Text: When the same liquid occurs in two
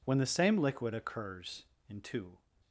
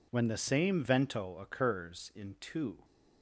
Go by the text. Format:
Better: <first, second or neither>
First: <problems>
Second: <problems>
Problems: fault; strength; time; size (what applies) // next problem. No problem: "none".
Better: first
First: none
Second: says "vento" for "liquid"; at 0.8 s